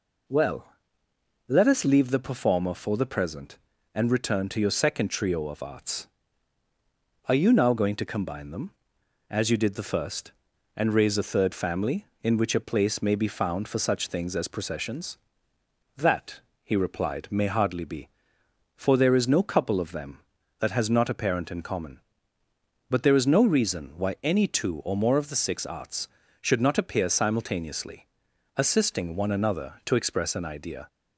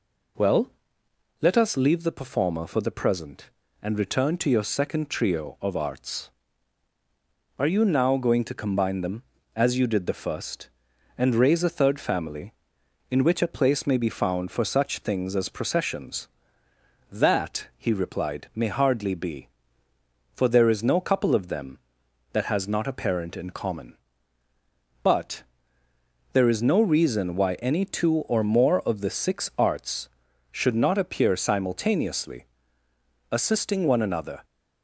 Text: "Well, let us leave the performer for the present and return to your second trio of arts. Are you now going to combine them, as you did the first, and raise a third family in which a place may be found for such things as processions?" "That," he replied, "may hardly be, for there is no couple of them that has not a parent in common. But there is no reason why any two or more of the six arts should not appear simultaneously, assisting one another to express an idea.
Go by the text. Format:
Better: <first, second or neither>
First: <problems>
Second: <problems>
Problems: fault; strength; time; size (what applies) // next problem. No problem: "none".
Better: first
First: none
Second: pauses between "But" and "there"; noticeable; at 25.4 s; 0.90 s long // stops before "to express an idea"; at 34.4 s